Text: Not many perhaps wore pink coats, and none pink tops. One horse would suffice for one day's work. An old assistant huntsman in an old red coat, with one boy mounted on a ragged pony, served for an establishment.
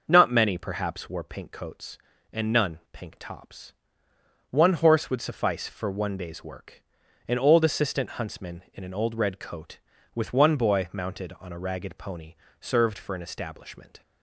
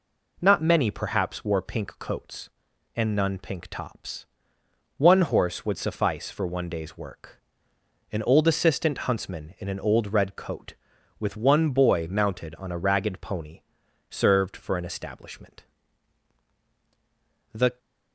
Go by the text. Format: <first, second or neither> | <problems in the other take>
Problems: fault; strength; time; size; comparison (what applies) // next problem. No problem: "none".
first | goes on to say "The"; slight; from 17.5 s on; 0.26 s long